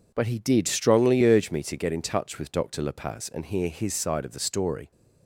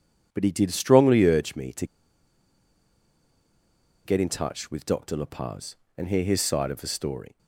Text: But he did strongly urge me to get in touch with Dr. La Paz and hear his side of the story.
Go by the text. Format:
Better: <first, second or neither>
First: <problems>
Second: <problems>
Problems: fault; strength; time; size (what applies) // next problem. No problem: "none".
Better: first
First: none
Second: pauses between "to" and "get"; strong; at 1.8 s; 2.1 s long